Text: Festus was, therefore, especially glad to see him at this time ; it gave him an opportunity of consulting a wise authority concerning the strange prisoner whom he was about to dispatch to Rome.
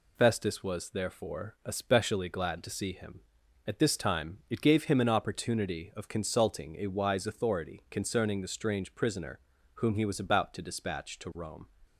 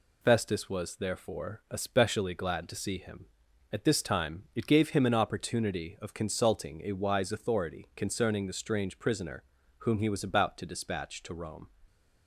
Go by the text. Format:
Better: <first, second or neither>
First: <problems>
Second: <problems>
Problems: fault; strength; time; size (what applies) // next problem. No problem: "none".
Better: neither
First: pauses between "prisoner" and "whom"; at 9.3 s; 0.38 s long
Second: pauses between "prisoner" and "whom"; at 9.4 s; 0.38 s long